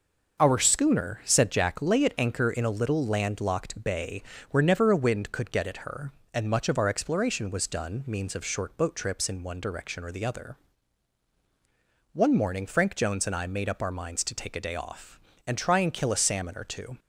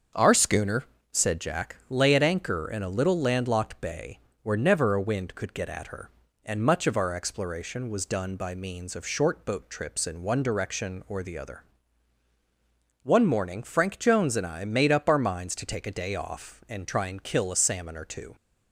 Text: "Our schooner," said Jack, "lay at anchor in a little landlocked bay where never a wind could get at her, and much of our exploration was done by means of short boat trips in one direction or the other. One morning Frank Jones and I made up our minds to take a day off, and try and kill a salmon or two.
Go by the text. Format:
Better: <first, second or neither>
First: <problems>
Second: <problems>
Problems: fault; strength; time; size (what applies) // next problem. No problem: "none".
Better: second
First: starts louder than the rest; until 1.4 s; 6 dB // pauses between "bay" and "where"; slight; at 4.2 s; 0.30 s long // skips "by"; at 8.0 s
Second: starts louder than the rest; until 1.4 s; 7 dB // pauses between "bay" and "where"; slight; at 4.1 s; 0.24 s long